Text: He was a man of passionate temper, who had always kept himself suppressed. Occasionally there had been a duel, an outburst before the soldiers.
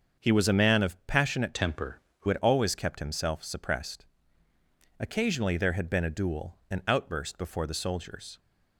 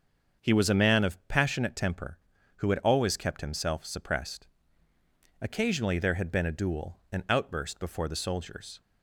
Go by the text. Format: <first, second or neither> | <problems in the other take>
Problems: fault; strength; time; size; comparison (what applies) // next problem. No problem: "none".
second | starts louder than the rest; until 1.3 s; 7 dB; also in the second // changes voice from "temper" to "who"; from 1.5 to 2.2 s; 0.7 s long